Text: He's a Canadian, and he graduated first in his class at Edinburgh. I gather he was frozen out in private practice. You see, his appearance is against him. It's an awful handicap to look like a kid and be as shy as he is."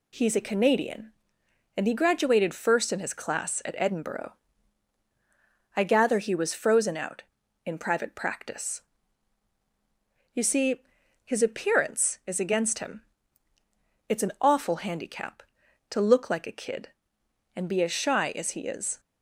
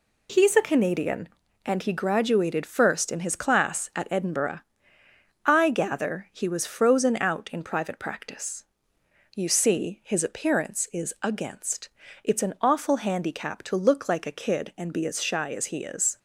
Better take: first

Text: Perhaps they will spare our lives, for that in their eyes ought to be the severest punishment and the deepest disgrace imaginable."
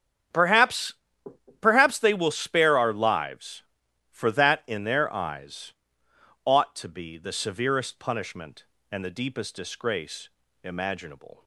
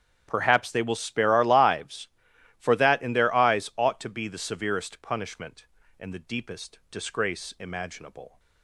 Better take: second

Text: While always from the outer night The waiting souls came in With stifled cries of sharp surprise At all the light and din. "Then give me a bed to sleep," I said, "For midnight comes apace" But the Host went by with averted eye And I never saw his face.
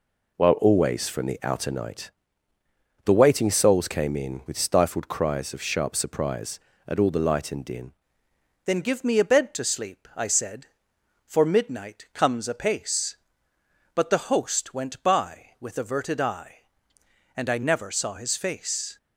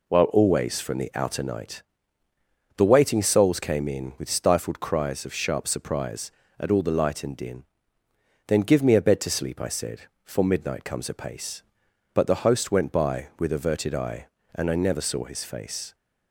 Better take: second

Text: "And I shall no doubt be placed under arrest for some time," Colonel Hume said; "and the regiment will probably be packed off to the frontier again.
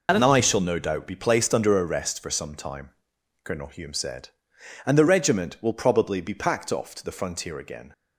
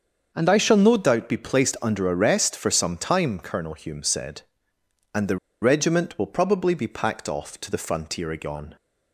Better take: first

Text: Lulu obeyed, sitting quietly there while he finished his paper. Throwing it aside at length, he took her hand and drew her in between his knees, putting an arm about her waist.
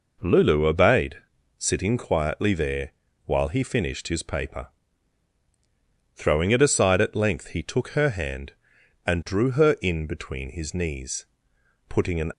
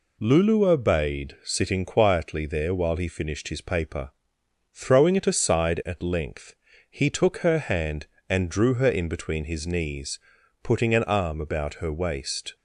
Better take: second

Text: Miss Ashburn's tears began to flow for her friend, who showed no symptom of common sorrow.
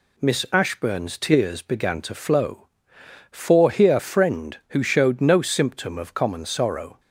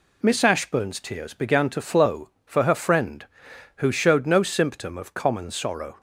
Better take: second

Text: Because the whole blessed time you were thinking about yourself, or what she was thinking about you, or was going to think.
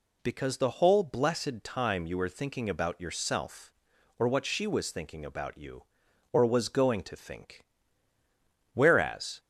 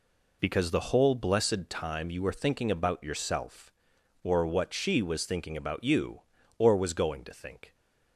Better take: second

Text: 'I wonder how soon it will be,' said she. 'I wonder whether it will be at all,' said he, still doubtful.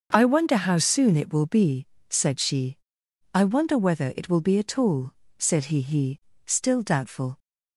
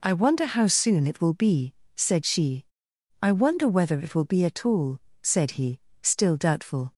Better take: second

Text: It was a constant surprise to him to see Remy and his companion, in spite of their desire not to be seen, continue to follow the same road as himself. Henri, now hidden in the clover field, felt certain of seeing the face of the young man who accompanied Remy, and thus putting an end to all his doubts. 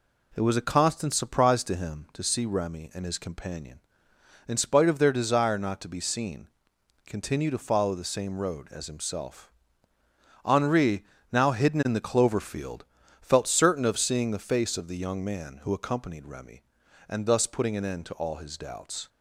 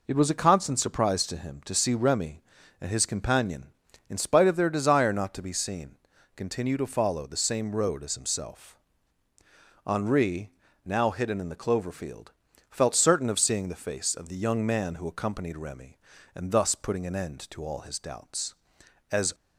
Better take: first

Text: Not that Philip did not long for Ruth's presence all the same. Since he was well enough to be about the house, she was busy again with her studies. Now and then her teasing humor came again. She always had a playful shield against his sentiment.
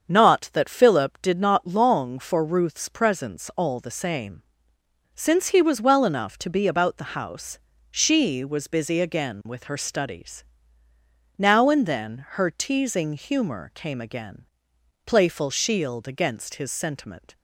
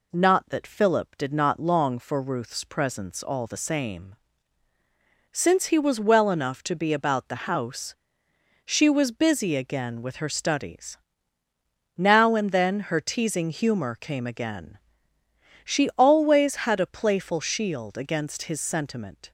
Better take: second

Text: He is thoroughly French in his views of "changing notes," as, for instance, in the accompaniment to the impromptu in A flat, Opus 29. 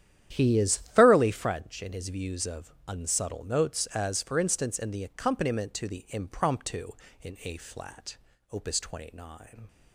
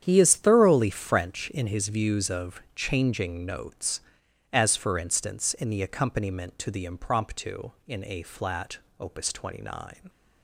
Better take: second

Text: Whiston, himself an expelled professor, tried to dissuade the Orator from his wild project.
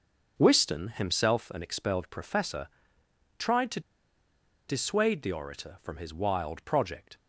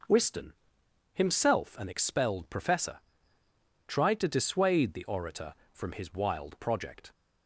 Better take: second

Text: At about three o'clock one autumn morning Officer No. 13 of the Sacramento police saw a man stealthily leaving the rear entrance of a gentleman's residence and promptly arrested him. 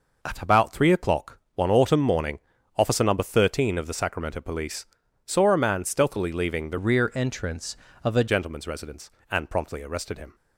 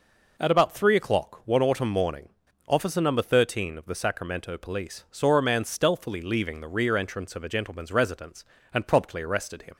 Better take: second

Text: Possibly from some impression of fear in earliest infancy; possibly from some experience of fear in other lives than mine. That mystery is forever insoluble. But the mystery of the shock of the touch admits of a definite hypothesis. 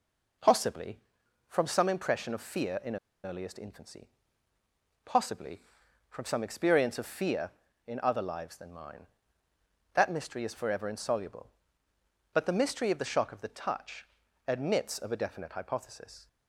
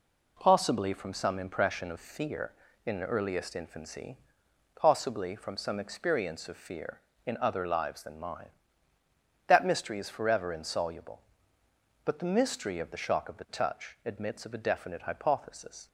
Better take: second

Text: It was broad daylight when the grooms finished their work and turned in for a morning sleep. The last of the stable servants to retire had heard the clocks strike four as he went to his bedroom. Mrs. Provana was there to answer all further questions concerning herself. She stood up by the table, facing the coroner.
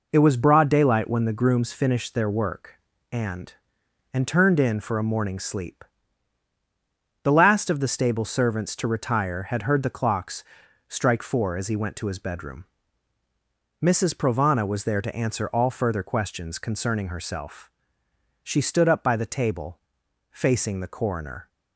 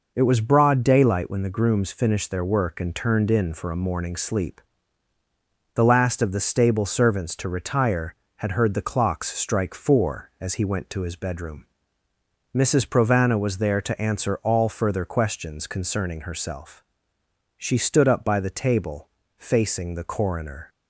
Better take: second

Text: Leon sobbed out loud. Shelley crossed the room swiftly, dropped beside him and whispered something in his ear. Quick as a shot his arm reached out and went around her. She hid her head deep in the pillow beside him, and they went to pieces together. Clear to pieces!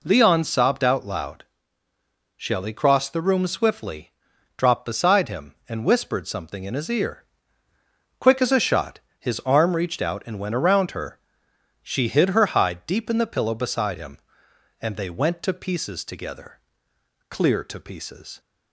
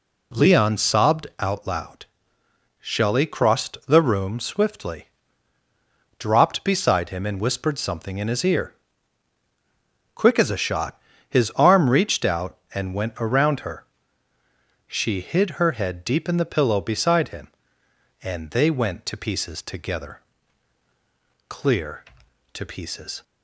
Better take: second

